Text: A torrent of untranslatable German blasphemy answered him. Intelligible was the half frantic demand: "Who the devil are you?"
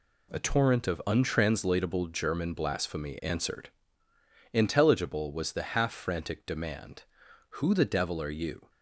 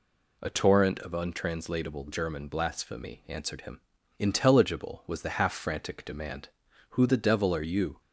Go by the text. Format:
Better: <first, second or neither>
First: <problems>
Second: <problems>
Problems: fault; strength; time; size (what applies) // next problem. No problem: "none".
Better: second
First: skips "him"; at 4.1 s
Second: none